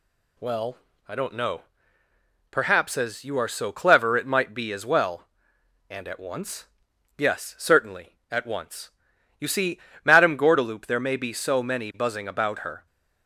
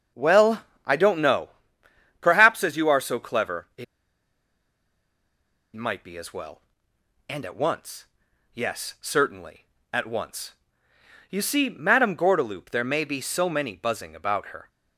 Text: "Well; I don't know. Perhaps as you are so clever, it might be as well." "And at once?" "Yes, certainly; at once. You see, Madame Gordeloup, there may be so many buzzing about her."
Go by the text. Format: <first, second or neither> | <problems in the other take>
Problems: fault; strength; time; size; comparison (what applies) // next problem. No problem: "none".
first | starts louder than the rest; until 1.3 s; 6.5 dB // pauses between "it" and "might"; strong; at 3.8 s; 1.9 s long